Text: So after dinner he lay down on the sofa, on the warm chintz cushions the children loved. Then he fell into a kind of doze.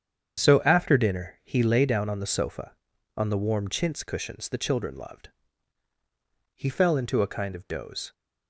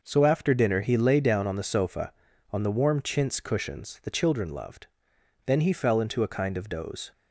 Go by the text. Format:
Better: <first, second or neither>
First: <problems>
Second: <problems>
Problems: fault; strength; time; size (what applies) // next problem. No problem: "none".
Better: second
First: starts louder than the rest; strong; until 1.4 s; 8 dB // skips "Then"; at 5.9 s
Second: none